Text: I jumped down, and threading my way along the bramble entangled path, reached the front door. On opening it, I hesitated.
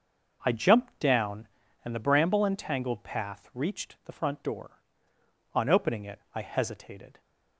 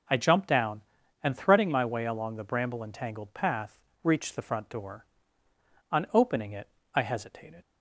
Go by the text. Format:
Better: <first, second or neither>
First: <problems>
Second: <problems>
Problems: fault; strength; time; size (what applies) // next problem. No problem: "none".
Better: second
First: starts louder than the rest; noticeable; until 1.4 s; 6 dB // skips "threading my way along"; at 1.9 s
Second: none